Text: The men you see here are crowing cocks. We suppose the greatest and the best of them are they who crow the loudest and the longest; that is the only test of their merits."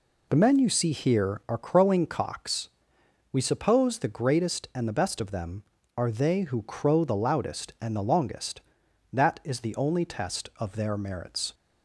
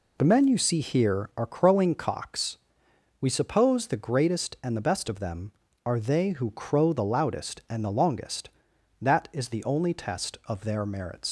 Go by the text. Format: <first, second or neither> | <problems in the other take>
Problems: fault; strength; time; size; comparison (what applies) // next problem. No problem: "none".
first | leaves "merits" unfinished; at 11.2 s; 110 ms